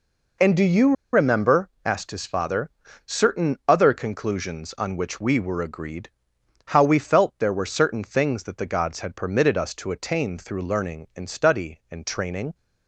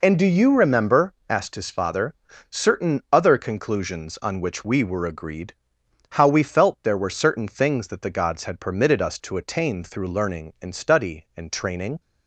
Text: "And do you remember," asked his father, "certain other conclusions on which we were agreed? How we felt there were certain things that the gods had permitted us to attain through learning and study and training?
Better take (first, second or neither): second